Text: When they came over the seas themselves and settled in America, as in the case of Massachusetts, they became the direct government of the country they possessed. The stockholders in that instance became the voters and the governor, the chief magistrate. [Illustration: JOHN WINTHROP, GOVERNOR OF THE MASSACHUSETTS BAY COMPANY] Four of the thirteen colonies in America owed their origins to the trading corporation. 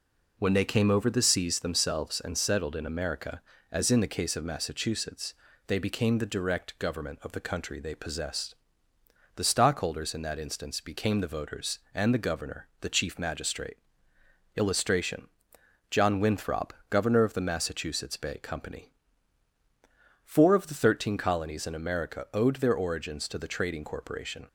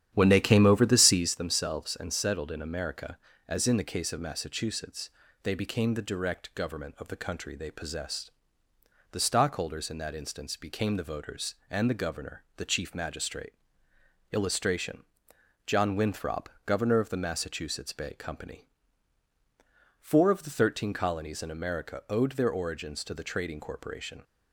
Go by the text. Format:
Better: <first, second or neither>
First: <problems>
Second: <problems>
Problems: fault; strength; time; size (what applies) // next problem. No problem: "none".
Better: first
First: pauses between "COMPANY" and "Four"; strong; at 18.9 s; 1.3 s long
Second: starts louder than the rest; strong; until 1.4 s; 10.5 dB // pauses between "COMPANY" and "Four"; strong; at 18.6 s; 1.3 s long